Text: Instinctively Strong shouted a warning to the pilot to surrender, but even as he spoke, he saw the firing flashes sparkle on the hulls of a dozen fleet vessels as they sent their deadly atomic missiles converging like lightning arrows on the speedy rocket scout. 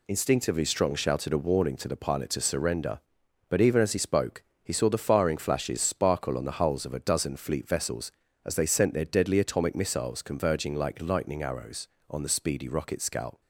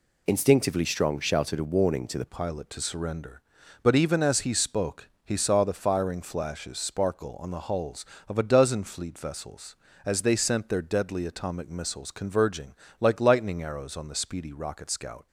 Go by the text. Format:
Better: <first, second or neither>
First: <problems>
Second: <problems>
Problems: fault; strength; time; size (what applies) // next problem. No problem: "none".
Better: first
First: none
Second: changes voice at "pilot"; from 2.2 s on; 13.0 s long // pauses between "converging" and "like"; slight; at 12.7 s; 0.26 s long